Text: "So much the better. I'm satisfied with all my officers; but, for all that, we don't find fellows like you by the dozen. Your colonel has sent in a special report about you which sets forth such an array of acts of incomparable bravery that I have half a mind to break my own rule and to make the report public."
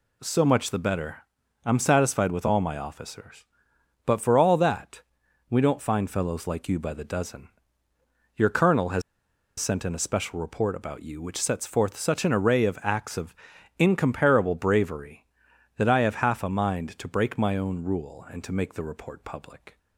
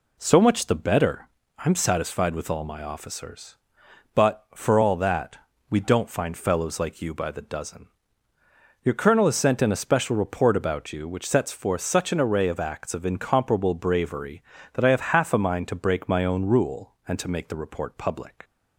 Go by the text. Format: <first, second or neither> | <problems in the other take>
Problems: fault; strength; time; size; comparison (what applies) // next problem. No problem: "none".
second | pauses between "has" and "sent"; noticeable; at 9.0 s; 0.57 s long // pauses between "of" and "incomparable"; at 13.3 s; 0.42 s long